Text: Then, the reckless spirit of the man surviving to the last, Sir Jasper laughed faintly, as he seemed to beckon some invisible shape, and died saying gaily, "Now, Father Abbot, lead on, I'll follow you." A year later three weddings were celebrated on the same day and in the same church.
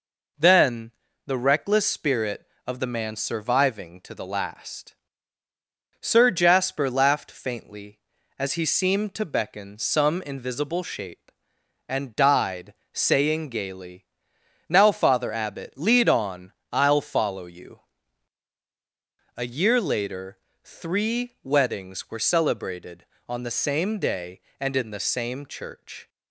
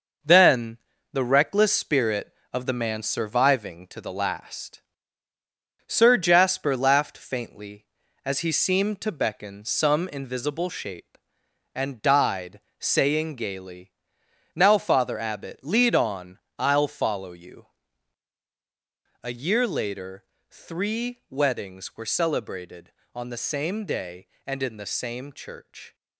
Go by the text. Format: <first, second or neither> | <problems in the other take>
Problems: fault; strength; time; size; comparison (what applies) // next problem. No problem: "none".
first | gets quieter; noticeable; throughout; 6 dB // pauses between "died" and "saying"; slight; at 12.6 s; 0.18 s long; slight in the first // pauses between "later" and "three"; slight; at 20.2 s; 0.26 s long; slight in the first